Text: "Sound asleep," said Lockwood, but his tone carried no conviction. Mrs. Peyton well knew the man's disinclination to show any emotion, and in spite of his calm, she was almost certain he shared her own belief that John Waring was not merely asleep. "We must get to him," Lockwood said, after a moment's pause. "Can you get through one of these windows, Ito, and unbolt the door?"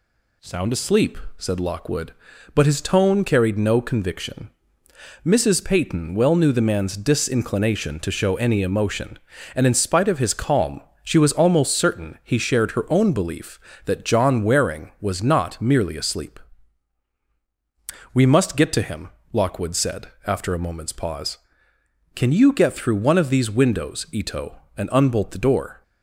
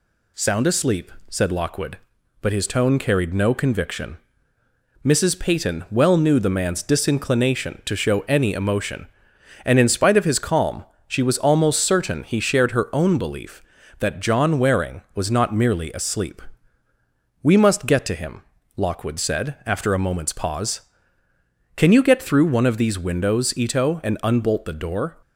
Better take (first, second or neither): neither